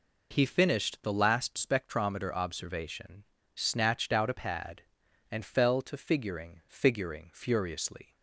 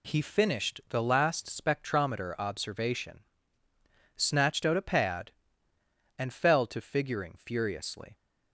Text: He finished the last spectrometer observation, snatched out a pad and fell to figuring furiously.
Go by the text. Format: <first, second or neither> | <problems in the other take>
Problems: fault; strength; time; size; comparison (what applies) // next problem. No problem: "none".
second | says "figuring" twice; at 6.6 s